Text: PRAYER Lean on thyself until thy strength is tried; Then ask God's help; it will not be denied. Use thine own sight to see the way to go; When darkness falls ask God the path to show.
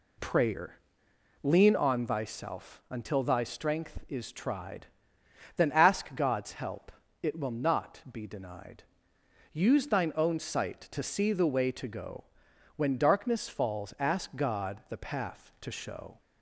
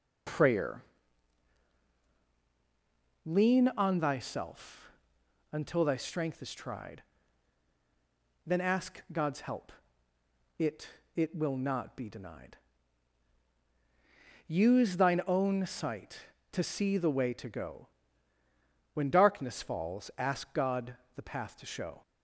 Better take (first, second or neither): first